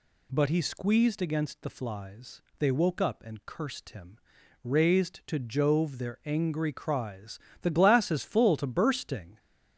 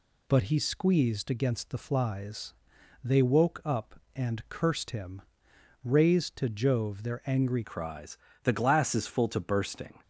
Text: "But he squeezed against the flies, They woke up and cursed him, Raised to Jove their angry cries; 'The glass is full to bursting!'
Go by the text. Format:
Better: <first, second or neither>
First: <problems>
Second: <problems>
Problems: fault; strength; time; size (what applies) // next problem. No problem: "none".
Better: first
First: none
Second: changes voice at "cries"; from 7.6 s on; 2.4 s long